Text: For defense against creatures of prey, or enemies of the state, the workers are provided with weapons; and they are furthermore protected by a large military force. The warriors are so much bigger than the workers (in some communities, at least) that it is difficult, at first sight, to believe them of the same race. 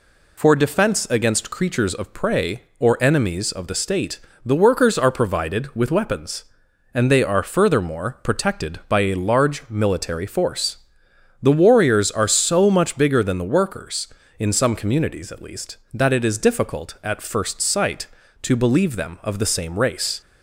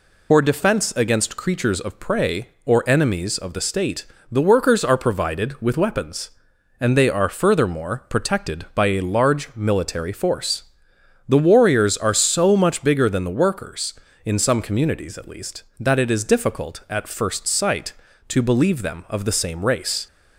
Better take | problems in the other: first | loses the start of "For"; at 0.3 s; 65 ms

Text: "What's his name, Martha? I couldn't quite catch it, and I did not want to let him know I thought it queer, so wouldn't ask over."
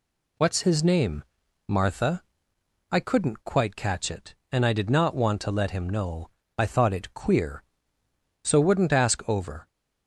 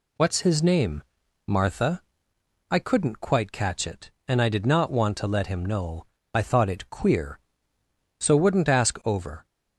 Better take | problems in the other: neither | pauses between "know" and "I"; slight; the same in both

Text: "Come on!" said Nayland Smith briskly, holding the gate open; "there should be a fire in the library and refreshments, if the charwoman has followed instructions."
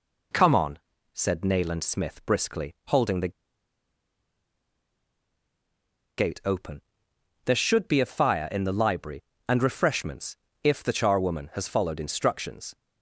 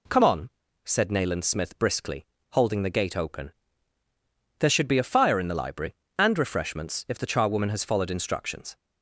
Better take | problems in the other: second | pauses between "the" and "gate"; strong; at 3.3 s; 2.8 s long

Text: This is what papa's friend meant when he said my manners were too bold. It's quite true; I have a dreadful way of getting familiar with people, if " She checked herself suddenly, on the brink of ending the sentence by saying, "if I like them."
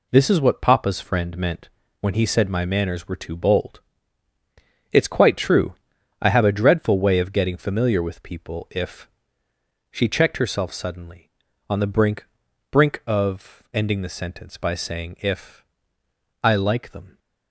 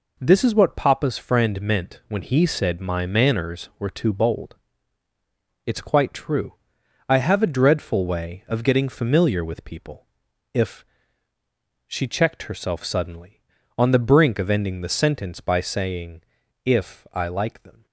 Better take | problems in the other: second | pauses between "meant" and "when"; slight; at 1.6 s; 0.32 s long // says "brink" twice; at 12.7 s // pauses between "if" and "I"; noticeable; at 15.6 s; 0.80 s long

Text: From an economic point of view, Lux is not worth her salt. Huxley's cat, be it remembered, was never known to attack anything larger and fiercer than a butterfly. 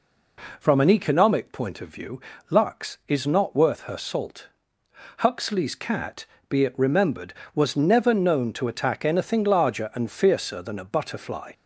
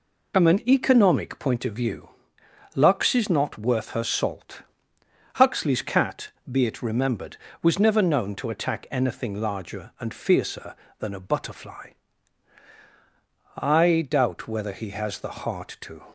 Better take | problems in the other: first | goes on to say "I doubt whether he has the heart to"; strong; from 13.5 s on; 2.4 s long

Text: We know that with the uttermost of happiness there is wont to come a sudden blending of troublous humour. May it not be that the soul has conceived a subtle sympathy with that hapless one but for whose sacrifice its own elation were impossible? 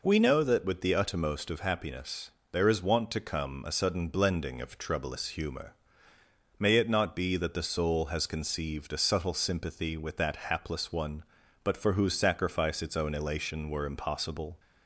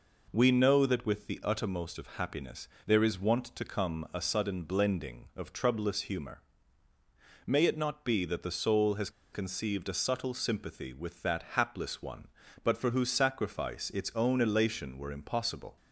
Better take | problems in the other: first | pauses between "happiness" and "there"; slight; at 2.6 s; 0.18 s long; slight in the first // pauses between "has" and "conceived"; slight; at 9.0 s; 0.23 s long

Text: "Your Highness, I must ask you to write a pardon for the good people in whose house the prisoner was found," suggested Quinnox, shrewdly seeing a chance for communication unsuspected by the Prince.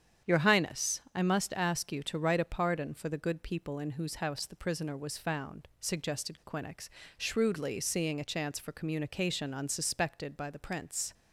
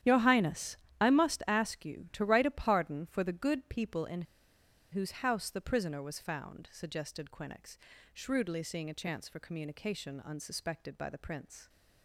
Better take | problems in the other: first | starts louder than the rest; strong; until 1.2 s; 11 dB; strong in the first // pauses between "in" and "whose"; noticeable; at 4.2 s; 0.69 s long

